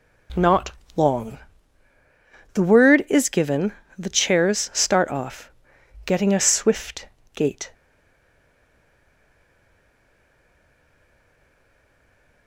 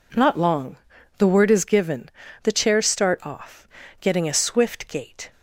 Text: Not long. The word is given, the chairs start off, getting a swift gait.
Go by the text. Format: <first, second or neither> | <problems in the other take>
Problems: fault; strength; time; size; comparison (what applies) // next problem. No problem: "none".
second | pauses between "Not" and "long"; slight; at 0.7 s; 0.24 s long // pauses between "swift" and "gait"; slight; at 7.0 s; 0.28 s long // stays silent after the last word; strong; from 7.7 s on; 4.7 s long